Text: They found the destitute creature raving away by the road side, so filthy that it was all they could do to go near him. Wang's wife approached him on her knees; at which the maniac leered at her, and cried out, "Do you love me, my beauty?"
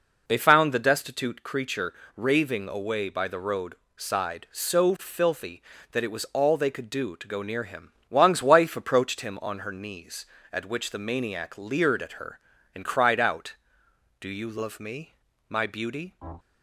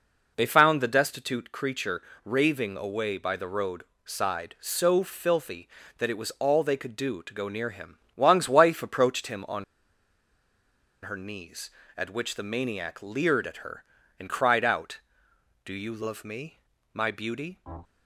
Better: first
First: pauses between "creature" and "raving"; slight; at 1.9 s; 0.22 s long // pauses between "road" and "side"; slight; at 3.7 s; 0.20 s long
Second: pauses between "creature" and "raving"; slight; at 2.0 s; 0.22 s long // pauses between "road" and "side"; slight; at 3.8 s; 0.20 s long // pauses between "on" and "her"; strong; at 9.6 s; 1.4 s long

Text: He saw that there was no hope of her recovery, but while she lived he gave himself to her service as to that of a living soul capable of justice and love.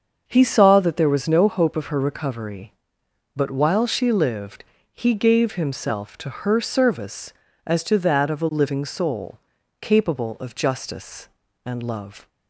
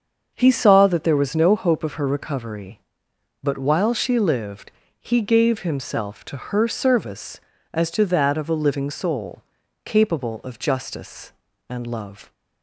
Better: neither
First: starts louder than the rest; until 1.2 s; 6.5 dB // pauses between "lived" and "he"; slight; at 4.6 s; 0.28 s long // pauses between "soul" and "capable"; at 9.3 s; 0.42 s long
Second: starts louder than the rest; until 1.3 s; 6.5 dB // pauses between "lived" and "he"; slight; at 4.7 s; 0.28 s long // pauses between "soul" and "capable"; at 9.4 s; 0.42 s long

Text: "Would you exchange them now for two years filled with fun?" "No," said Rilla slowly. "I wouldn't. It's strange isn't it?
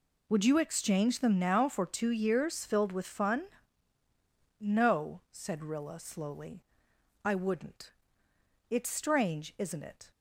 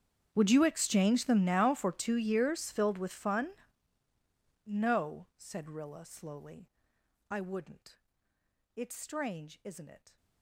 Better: first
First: none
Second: gets quieter; strong; throughout; 24.5 dB

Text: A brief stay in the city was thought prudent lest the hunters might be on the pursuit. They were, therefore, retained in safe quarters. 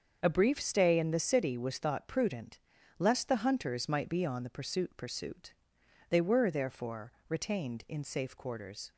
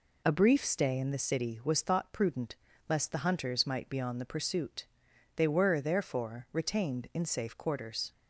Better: second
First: starts louder than the rest; until 1.2 s; 6.5 dB // pauses between "prudent" and "lest"; at 2.5 s; 0.38 s long // says "pursuit" twice; at 4.9 s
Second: pauses between "prudent" and "lest"; slight; at 2.5 s; 0.32 s long

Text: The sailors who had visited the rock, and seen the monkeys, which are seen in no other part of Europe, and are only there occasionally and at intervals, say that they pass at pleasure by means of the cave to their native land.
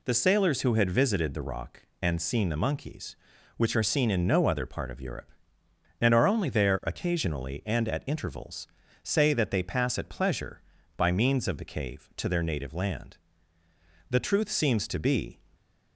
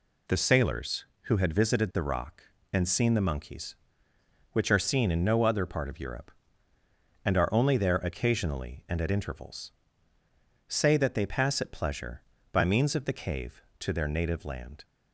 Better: second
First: goes on to say "The truth seems to be"; noticeable; from 14.1 s on; 1.2 s long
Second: none

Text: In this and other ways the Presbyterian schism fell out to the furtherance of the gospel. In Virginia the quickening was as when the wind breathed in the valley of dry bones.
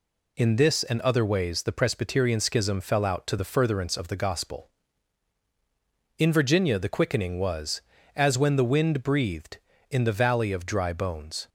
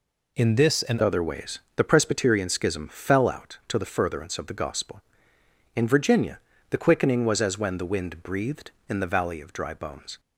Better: first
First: none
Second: changes voice at "other"; from 1.0 s on; 9.1 s long // pauses between "ways" and "the"; slight; at 1.5 s; 0.18 s long // pauses between "Virginia" and "the"; slight; at 6.3 s; 0.32 s long

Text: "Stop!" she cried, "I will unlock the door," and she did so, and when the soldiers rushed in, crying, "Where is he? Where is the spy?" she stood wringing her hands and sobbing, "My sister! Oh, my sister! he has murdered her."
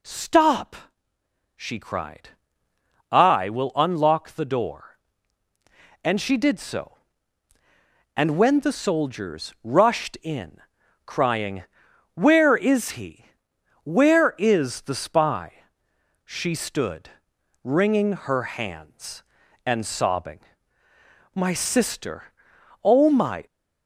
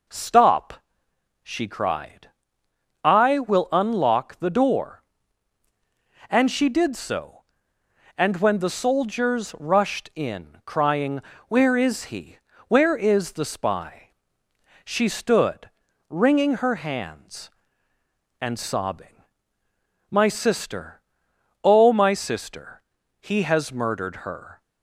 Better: second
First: pauses between "stood" and "wringing"; noticeable; at 17.0 s; 0.54 s long // stops before "sister he has murdered her"; at 23.4 s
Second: pauses between "stood" and "wringing"; at 15.6 s; 0.40 s long

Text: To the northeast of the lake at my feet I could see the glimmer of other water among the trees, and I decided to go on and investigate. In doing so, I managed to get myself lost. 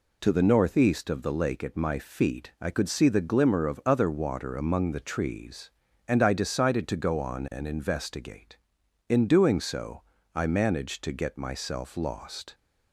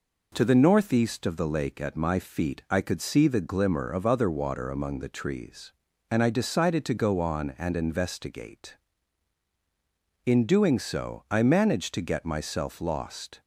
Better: neither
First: none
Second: none

